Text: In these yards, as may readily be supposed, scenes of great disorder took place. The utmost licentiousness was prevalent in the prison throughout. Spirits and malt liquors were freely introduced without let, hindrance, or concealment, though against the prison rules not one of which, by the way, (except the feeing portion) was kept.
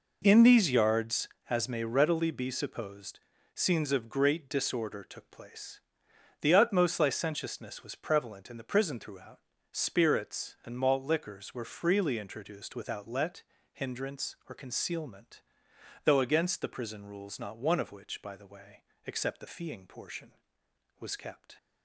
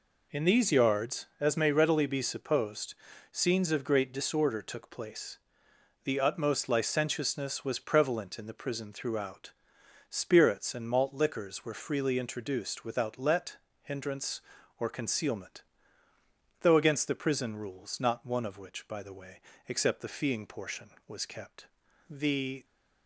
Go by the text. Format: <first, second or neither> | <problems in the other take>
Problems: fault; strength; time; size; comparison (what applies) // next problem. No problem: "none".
first | goes on to say "The"; from 22.1 s on; 0.54 s long